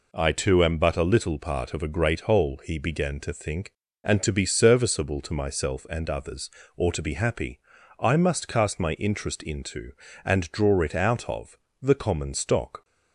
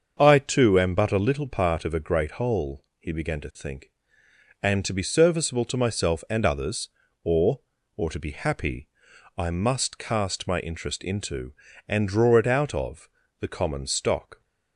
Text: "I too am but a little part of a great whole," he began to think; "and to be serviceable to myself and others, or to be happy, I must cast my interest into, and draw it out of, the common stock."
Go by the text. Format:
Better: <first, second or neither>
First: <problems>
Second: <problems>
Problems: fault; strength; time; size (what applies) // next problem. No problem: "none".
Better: first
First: none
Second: starts louder than the rest; until 1.1 s; 7 dB // says "or" twice; at 7.9 s